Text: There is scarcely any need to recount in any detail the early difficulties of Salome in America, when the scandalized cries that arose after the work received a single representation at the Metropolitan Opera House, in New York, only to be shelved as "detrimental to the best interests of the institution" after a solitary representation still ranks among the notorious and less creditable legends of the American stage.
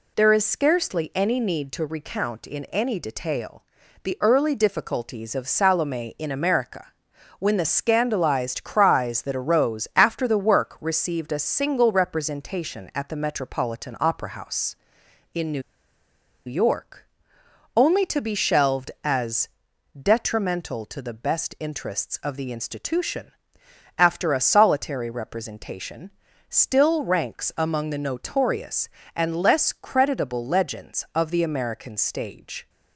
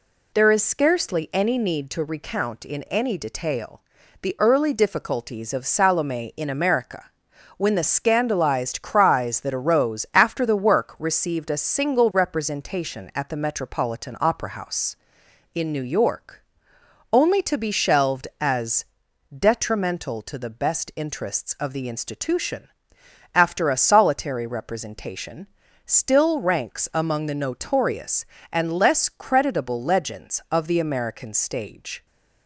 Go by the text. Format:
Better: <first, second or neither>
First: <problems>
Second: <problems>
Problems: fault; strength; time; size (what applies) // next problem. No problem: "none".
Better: second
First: pauses between "detail" and "the"; at 3.6 s; 0.40 s long // pauses between "New" and "York"; noticeable; at 15.6 s; 0.84 s long // pauses between "as" and "detrimental"; noticeable; at 19.4 s; 0.54 s long // pauses between "institution" and "after"; noticeable; at 23.3 s; 0.66 s long // pauses between "representation" and "still"; at 26.1 s; 0.40 s long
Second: pauses between "detail" and "the"; at 3.8 s; 0.40 s long // pauses between "as" and "detrimental"; noticeable; at 18.8 s; 0.54 s long // pauses between "institution" and "after"; noticeable; at 22.6 s; 0.66 s long // pauses between "representation" and "still"; at 25.4 s; 0.40 s long